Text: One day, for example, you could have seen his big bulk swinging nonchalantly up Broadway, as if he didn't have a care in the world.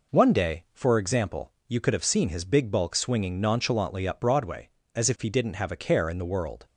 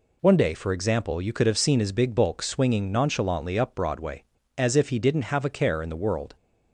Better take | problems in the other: neither | none

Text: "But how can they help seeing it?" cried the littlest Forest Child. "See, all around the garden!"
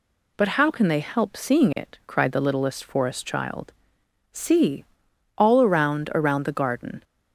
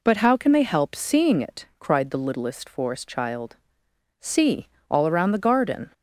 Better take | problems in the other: second | says "around" twice; at 6.1 s

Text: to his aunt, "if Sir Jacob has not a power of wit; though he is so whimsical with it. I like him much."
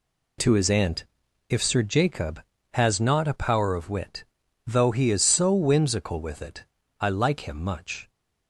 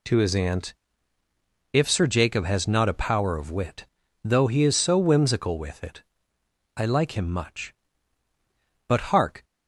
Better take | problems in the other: first | goes on to say "But hark"; from 8.8 s on; 0.56 s long

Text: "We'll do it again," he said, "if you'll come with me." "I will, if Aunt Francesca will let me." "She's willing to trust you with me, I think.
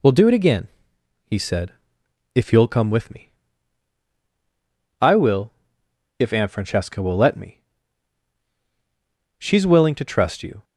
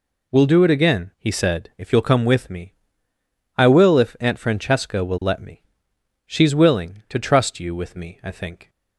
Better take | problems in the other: second | stops before "with me I think"; at 10.6 s

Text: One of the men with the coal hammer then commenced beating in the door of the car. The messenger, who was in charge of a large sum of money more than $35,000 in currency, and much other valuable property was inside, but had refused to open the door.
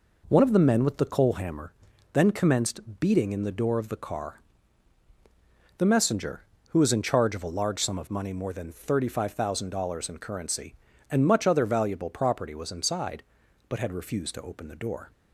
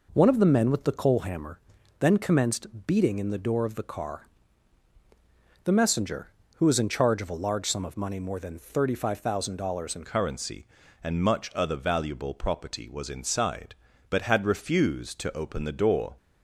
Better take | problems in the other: first | pauses between "hammer" and "then"; at 1.5 s; 0.40 s long; also in the first // changes voice at "currency"; from 10.0 s on; 6.1 s long

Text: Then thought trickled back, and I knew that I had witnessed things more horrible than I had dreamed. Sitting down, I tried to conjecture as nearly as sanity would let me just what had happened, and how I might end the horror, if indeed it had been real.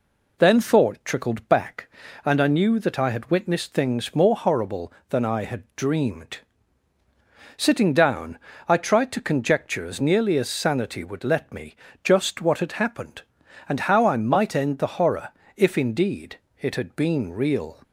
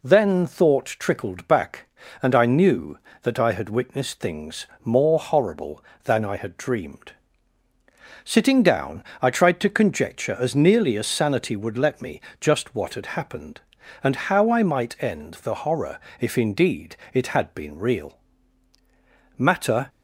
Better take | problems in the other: first | pauses between "things" and "more"; slight; at 4.6 s; 0.18 s long // pauses between "me" and "just"; slight; at 12.2 s; 0.20 s long; slight in the first // pauses between "indeed" and "it"; slight; at 16.9 s; 0.16 s long; slight in the first // goes on to say "Matter"; from 19.3 s on; 0.52 s long

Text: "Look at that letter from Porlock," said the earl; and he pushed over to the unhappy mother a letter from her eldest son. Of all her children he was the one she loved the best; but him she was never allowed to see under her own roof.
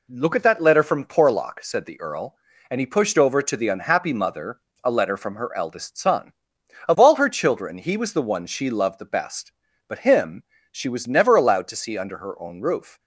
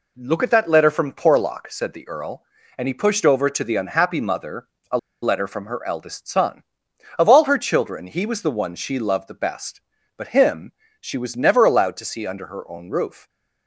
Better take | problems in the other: first | pauses between "mother" and "a"; slight; at 4.6 s; 0.24 s long; slight in the first // pauses between "a" and "letter"; slight; at 4.9 s; 0.24 s long // pauses between "him" and "she"; slight; at 10.7 s; 0.28 s long; slight in the first

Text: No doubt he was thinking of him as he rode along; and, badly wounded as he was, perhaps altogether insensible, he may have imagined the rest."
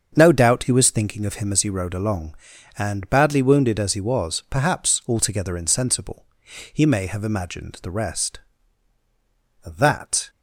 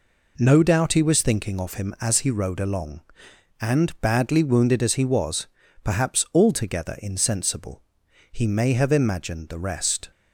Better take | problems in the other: second | starts louder than the rest; until 1.1 s; 7 dB // goes on to say "That"; noticeable; from 9.6 s on; 0.64 s long

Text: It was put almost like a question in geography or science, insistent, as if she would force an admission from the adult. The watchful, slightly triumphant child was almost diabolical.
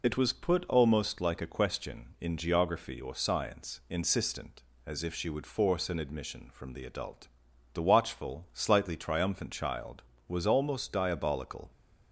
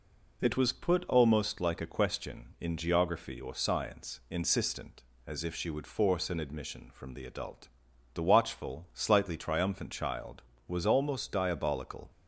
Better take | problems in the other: second | loses the start of "It"; at 0.0 s; 40 ms

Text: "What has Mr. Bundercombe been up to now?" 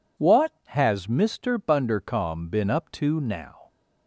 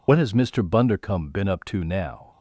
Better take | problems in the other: first | loses the start of "What"; at 0.0 s; 45 ms

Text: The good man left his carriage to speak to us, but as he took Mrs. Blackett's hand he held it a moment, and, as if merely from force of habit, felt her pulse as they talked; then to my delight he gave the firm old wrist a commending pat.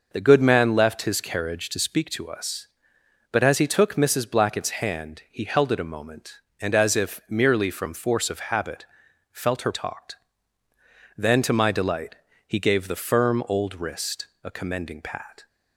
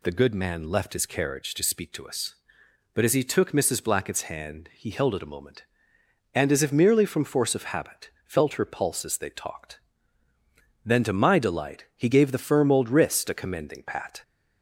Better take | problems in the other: second | skips "pulse as they"; at 9.7 s // pauses between "delight" and "he"; slight; at 12.1 s; 0.32 s long // pauses between "wrist" and "a"; slight; at 14.2 s; 0.16 s long

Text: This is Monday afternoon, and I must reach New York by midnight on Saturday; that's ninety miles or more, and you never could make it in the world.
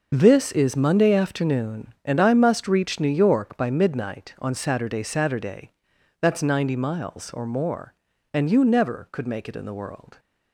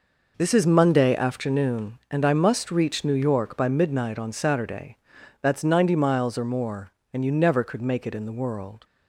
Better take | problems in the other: second | starts louder than the rest; noticeable; until 1.1 s; 6 dB // says "Saturday" twice; at 5.0 s

